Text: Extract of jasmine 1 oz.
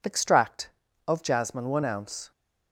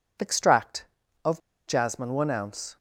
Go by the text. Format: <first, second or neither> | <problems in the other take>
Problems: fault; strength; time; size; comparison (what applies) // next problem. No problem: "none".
first | pauses between "of" and "jasmine"; slight; at 1.3 s; 0.29 s long